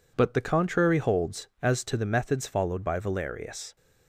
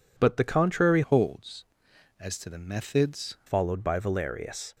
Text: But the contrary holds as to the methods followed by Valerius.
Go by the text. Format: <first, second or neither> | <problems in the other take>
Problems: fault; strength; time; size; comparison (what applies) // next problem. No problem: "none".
first | changes voice from "holds" to "methods"; from 1.0 to 3.3 s; 2.3 s long